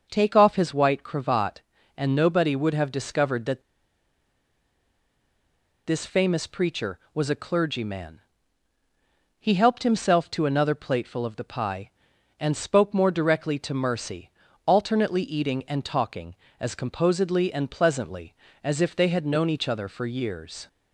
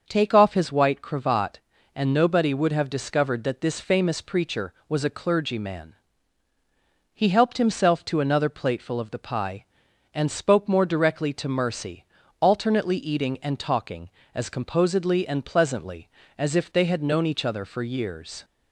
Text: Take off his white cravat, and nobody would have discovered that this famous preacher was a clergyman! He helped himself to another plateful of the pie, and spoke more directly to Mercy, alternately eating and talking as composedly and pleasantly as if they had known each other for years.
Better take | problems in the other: second | starts louder than the rest; until 1.1 s; 6 dB; also in the second // pauses between "that" and "this"; strong; at 3.6 s; 2.2 s long

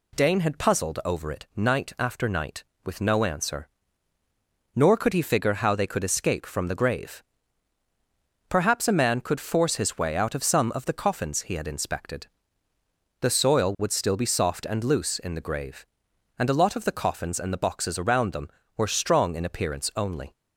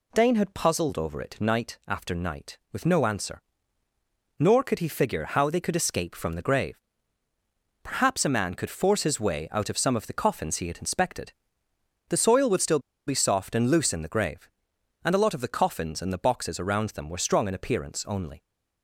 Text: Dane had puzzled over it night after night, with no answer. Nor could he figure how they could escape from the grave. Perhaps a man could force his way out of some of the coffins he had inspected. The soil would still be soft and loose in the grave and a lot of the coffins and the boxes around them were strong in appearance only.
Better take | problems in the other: first | pauses between "still" and "be"; slight; at 12.8 s; 0.26 s long

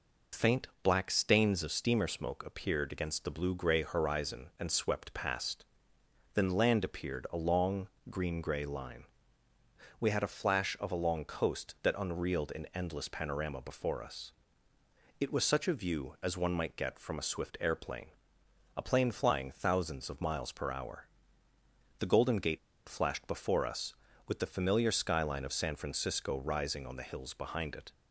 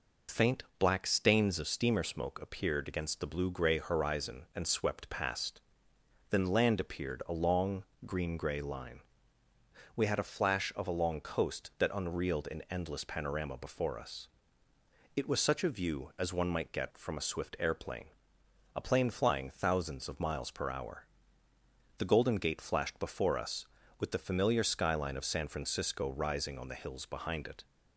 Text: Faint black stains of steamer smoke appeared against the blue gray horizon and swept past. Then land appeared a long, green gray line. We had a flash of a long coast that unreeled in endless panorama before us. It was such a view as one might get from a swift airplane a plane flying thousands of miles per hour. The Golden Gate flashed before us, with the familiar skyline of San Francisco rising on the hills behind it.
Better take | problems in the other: second | pauses between "Faint" and "black"; slight; at 0.6 s; 0.16 s long; slight in the second // pauses between "airplane" and "a"; noticeable; at 18.0 s; 0.68 s long; noticeable in the second // pauses between "Gate" and "flashed"; slight; at 22.5 s; 0.29 s long

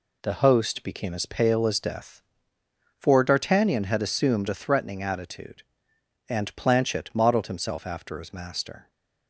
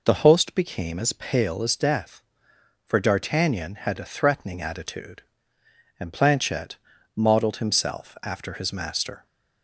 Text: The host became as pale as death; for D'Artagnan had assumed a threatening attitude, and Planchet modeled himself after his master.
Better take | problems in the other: first | skips "assumed"; at 3.9 s // pauses between "Planchet" and "modeled"; at 6.7 s; 0.38 s long

